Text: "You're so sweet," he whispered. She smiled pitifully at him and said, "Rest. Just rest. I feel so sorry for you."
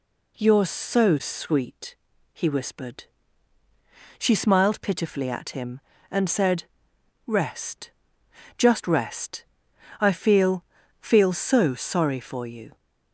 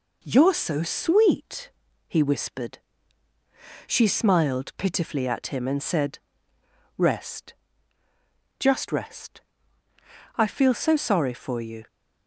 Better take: second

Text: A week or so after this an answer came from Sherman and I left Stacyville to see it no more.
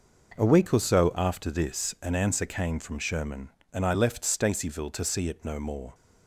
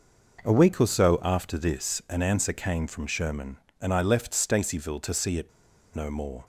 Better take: first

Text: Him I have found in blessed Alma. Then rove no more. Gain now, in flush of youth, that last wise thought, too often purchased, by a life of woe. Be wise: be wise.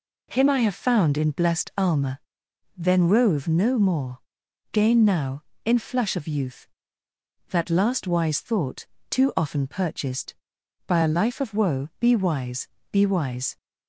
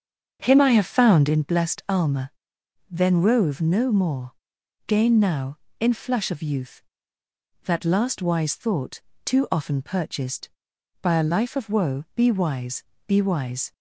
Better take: first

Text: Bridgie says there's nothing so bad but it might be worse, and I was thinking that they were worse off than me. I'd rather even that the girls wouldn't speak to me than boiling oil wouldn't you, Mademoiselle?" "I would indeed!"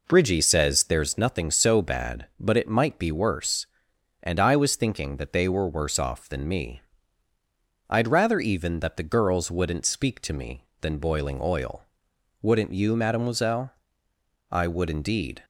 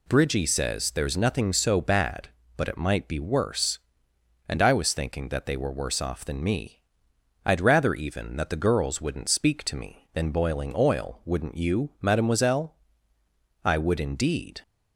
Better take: second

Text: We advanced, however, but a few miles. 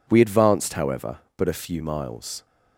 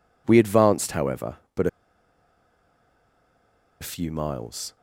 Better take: first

